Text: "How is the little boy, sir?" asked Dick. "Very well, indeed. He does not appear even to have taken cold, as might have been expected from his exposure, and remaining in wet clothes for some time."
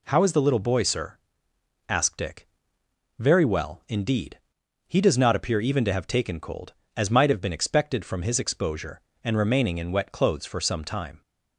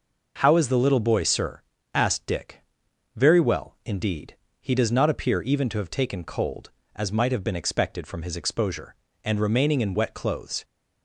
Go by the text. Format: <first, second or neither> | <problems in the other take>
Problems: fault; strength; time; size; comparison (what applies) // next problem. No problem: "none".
first | stops before "for some time"; at 10.6 s